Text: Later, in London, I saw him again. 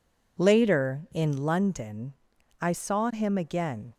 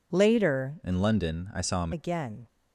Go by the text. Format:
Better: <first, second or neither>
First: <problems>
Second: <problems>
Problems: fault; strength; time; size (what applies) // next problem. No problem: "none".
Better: first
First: none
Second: changes voice from "in" to "him"; from 0.8 to 1.9 s; 1.1 s long